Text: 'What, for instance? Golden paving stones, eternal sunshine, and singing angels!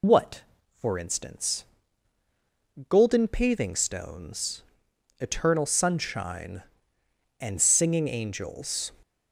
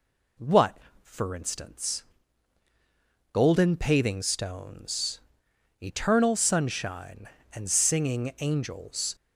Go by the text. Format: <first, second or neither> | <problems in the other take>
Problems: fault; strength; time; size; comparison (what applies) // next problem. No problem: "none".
second | loses the start of "What"; at 0.0 s; 85 ms